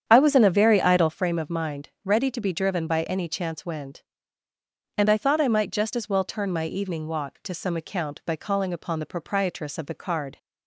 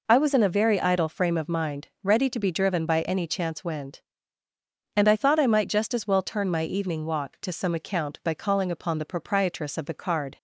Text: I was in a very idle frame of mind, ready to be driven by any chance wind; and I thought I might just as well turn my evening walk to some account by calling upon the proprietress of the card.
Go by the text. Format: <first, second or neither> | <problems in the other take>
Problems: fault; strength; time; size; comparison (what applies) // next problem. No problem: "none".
second | starts louder than the rest; strong; until 1.2 s; 8.5 dB